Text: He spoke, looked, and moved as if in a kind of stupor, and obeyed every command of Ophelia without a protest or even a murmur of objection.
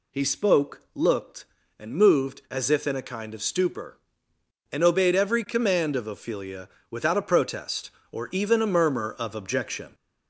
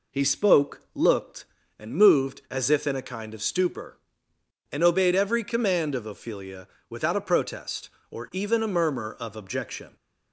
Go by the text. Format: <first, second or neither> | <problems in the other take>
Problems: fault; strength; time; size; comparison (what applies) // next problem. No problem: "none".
second | gets louder; slight; throughout; 3 dB // pauses between "Ophelia" and "without"; slight; at 6.6 s; 0.22 s long; slight in the second